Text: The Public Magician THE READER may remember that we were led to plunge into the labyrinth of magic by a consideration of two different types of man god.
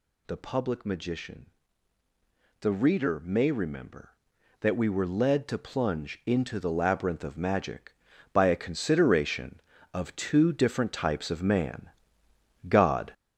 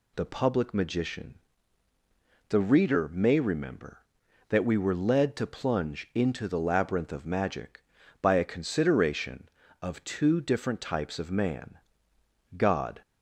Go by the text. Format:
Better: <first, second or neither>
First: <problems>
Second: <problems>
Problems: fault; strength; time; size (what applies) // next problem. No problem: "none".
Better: second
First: gets louder; noticeable; throughout; 5.5 dB // pauses between "Magician" and "THE"; at 1.4 s; 1.1 s long // pauses between "man" and "god"; noticeable; at 11.8 s; 0.80 s long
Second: pauses between "Magician" and "THE"; at 1.3 s; 1.1 s long // pauses between "man" and "god"; noticeable; at 11.7 s; 0.80 s long